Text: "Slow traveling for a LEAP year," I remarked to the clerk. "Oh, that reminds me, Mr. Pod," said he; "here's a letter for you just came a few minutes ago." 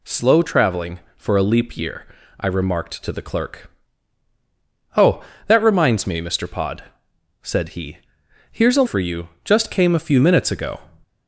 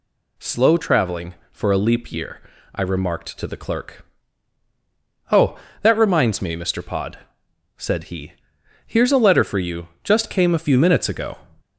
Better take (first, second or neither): second